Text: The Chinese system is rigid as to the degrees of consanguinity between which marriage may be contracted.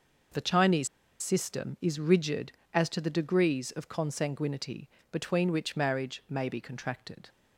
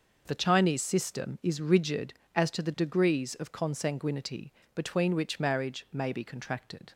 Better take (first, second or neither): second